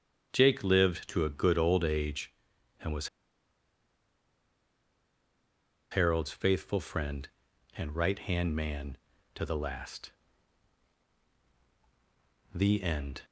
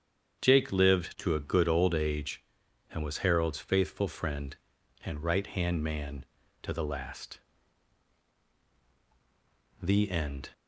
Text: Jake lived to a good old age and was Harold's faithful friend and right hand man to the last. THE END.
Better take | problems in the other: second | starts louder than the rest; strong; until 1.3 s; 8 dB; strong in the second // pauses between "was" and "Harold's"; strong; at 3.0 s; 2.8 s long

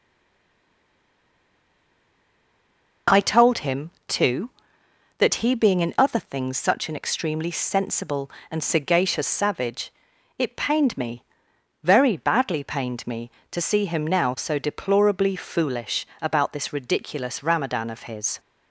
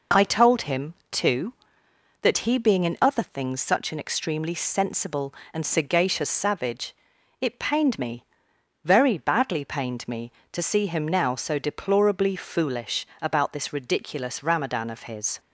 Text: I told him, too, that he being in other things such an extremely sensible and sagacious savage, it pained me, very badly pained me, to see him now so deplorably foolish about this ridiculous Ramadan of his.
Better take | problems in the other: second | stays silent before the first word; strong; until 3.0 s; 3.0 s long // pauses between "foolish" and "about"; slight; at 16.0 s; 0.16 s long; slight in the second

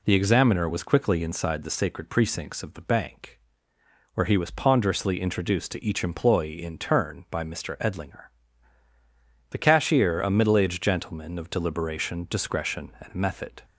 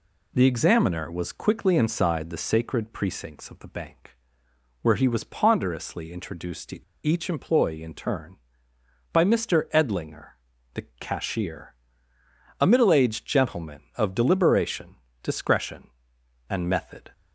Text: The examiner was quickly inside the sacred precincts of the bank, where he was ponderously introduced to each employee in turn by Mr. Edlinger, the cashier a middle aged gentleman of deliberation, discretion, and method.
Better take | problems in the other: first | pauses between "to" and "each"; slight; at 6.8 s; 0.22 s long // pauses between "the" and "cashier"; slight; at 10.8 s; 0.16 s long // pauses between "cashier" and "a"; noticeable; at 11.7 s; 0.88 s long

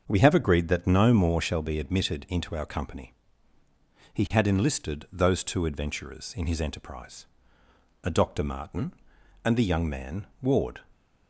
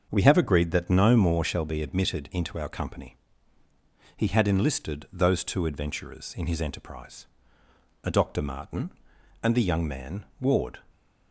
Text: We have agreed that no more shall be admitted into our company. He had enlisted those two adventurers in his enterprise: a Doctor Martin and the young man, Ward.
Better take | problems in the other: neither | starts louder than the rest; the same in both

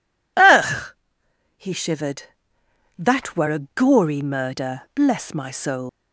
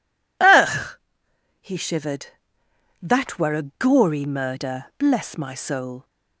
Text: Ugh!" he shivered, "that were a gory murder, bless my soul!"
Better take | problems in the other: second | leaves "soul" unfinished; at 5.8 s; 135 ms

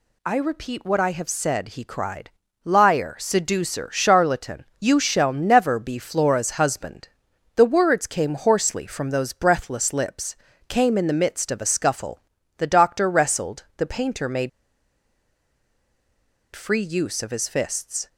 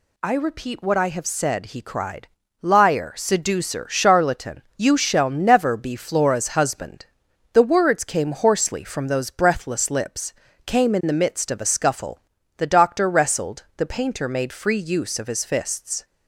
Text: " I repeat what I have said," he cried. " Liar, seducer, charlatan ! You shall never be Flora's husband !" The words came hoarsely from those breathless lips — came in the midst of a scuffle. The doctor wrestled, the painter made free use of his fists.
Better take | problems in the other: second | pauses between "made" and "free"; strong; at 14.4 s; 2.0 s long

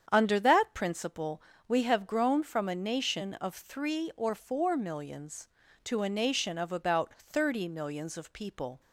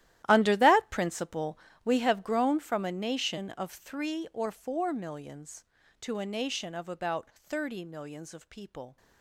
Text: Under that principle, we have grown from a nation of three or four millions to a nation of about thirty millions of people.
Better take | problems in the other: first | gets quieter; strong; throughout; 17.5 dB // starts louder than the rest; strong; until 1.3 s; 13.5 dB; strong in the first

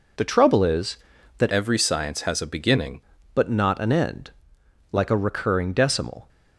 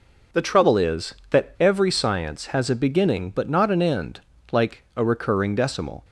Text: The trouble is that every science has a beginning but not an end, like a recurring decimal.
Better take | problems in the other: second | changes voice from "every" to "beginning"; from 1.4 to 2.9 s; 1.5 s long

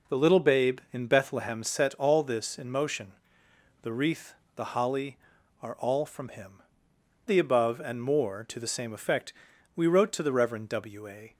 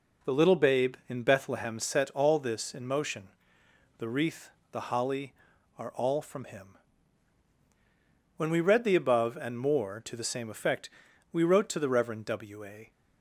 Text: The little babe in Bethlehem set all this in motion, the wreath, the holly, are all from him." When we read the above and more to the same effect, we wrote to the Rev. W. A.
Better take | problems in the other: second | skips "When we read"; at 6.9 s

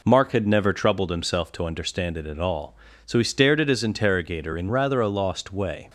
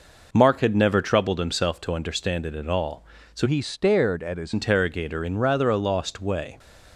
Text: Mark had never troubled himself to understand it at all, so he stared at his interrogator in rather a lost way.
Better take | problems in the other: first | changes voice from "he" to "his"; from 3.4 to 4.5 s; 1.1 s long

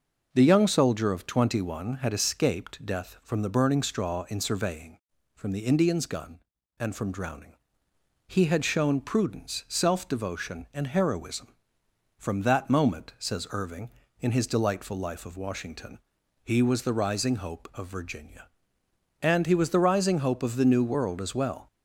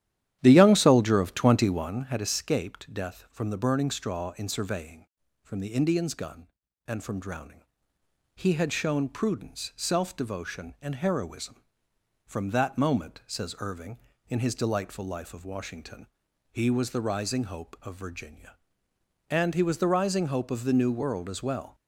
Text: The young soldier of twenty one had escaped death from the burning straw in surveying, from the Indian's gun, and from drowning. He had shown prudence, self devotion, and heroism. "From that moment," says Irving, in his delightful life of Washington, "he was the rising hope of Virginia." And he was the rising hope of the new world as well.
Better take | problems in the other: first | starts louder than the rest; strong; until 2.1 s; 11.5 dB

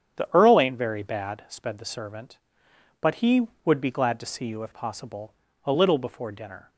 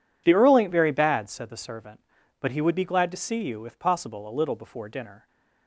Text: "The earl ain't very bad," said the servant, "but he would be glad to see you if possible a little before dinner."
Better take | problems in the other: second | starts louder than the rest; strong; until 1.2 s; 9 dB // says "sped" for "said"; at 1.4 s // pauses between "possible" and "a"; slight; at 5.3 s; 0.32 s long

